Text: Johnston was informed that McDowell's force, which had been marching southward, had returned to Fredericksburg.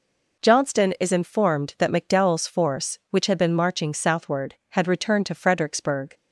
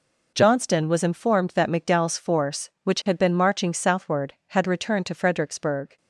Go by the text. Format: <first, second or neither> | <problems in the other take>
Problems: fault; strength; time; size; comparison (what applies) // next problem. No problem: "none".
second | says "is" for "was"; at 0.9 s